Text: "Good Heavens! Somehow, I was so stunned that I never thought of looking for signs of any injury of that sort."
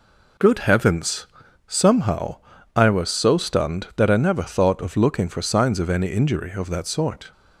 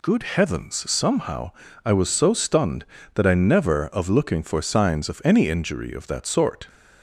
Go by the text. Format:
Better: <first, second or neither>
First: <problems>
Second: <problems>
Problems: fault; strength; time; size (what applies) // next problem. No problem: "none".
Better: first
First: none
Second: skips "thought"; at 3.8 s